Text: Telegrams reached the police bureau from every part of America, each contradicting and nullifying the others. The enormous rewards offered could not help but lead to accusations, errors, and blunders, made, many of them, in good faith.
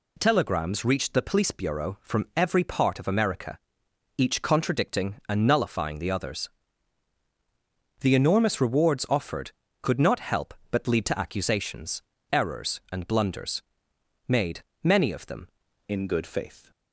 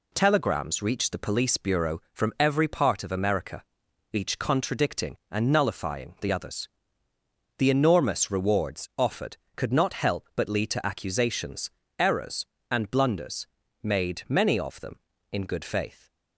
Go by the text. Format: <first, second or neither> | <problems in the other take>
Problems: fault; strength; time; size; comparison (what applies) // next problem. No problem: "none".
second | changes voice at "in"; from 15.8 s on; 0.9 s long